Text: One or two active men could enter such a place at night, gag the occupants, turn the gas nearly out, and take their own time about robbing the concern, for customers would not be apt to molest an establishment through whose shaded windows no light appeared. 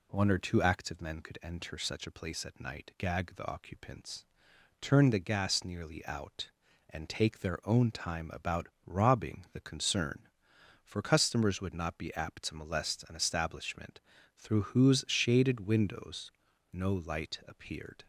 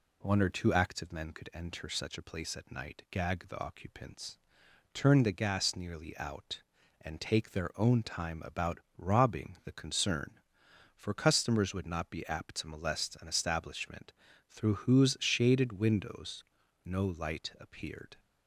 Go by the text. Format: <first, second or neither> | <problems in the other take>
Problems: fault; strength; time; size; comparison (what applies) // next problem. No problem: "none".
neither | pauses between "about" and "robbing"; slight; the same in both // pauses between "establishment" and "through"; the same in both // pauses between "windows" and "no"; the same in both